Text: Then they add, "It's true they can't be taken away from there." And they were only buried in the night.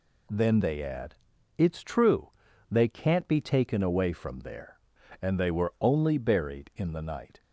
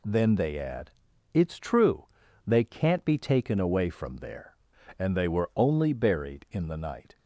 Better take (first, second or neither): neither